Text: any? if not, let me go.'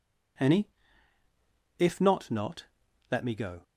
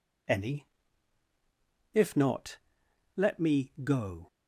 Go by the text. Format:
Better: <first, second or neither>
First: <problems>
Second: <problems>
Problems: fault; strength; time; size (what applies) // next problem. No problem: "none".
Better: second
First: says "not" twice; at 2.2 s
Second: none